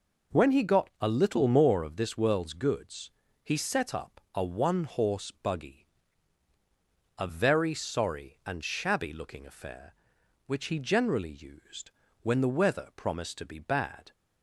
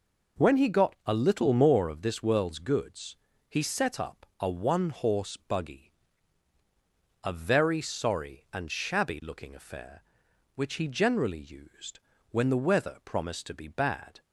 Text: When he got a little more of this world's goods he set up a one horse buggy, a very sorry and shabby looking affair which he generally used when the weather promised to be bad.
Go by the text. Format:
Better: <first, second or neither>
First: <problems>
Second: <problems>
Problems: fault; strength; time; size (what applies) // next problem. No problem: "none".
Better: neither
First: pauses between "goods" and "he"; slight; at 3.0 s; 0.34 s long // pauses between "used" and "when"; slight; at 11.8 s; 0.32 s long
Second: pauses between "goods" and "he"; slight; at 3.1 s; 0.34 s long // pauses between "used" and "when"; slight; at 11.9 s; 0.32 s long